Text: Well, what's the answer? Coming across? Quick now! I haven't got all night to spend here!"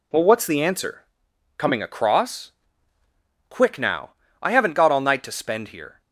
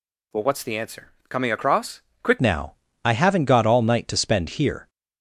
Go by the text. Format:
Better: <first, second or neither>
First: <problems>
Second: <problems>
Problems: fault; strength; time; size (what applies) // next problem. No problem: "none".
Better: first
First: none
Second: changes voice at "now"; from 2.3 s on; 2.5 s long